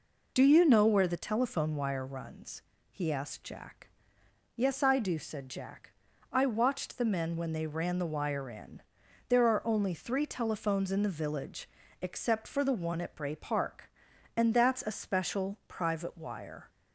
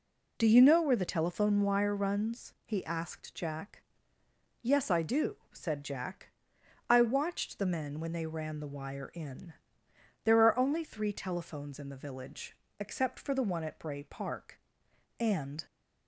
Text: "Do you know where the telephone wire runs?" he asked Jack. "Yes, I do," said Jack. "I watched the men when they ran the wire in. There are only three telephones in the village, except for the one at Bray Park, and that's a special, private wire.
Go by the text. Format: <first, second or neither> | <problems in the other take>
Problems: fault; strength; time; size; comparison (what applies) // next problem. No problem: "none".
first | stops before "that's a special private wire"; at 15.6 s